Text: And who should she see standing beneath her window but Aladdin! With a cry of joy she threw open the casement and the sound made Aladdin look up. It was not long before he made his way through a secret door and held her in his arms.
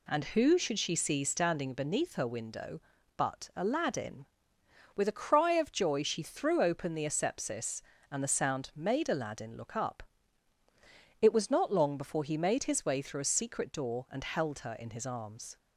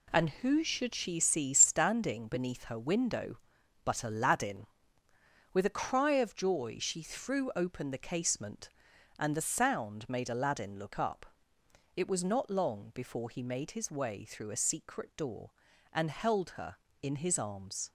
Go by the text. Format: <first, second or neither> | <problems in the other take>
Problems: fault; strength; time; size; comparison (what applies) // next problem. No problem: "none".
second | says "asepsis" for "casement"; at 7.0 s